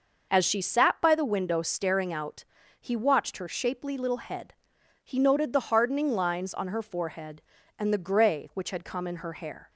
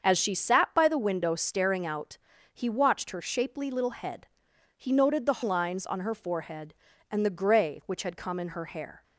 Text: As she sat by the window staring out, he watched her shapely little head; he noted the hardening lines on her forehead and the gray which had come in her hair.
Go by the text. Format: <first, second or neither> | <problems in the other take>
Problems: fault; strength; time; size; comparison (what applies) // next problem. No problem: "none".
first | starts louder than the rest; until 1.0 s; 7 dB // skips "hardening"; at 5.4 s